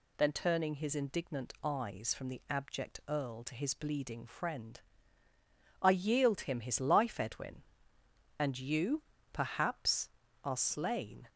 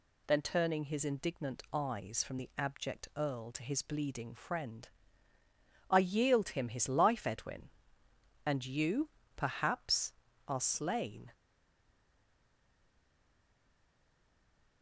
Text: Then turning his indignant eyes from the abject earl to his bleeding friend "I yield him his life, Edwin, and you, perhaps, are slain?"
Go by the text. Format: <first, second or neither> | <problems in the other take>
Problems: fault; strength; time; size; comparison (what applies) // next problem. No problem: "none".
first | pauses between "friend" and "I"; at 4.8 s; 1.0 s long; also in the first // stays silent after the last word; strong; from 11.3 s on; 3.5 s long